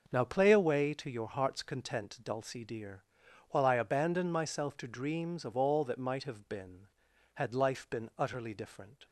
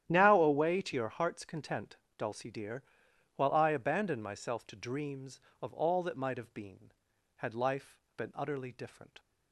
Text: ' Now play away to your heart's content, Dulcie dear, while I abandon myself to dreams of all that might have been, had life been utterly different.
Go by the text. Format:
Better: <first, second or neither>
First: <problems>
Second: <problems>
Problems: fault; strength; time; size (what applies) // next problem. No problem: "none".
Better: first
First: none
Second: starts louder than the rest; strong; until 1.0 s; 11 dB // skips "play"; at 0.4 s // pauses between "life" and "been"; slight; at 7.9 s; 0.16 s long